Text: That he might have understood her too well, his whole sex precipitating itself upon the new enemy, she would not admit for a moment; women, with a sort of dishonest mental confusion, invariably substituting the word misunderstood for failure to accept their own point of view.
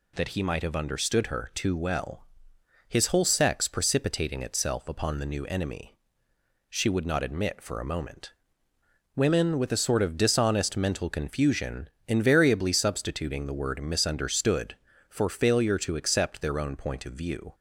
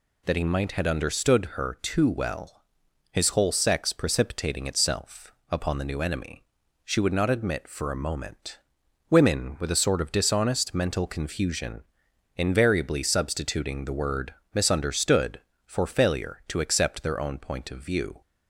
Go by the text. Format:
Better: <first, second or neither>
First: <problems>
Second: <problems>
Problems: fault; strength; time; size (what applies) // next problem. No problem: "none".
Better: first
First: none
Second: says "had" for "have"; at 0.7 s // pauses between "itself" and "upon"; slight; at 5.3 s; 0.18 s long // pauses between "word" and "misunderstood"; slight; at 14.3 s; 0.20 s long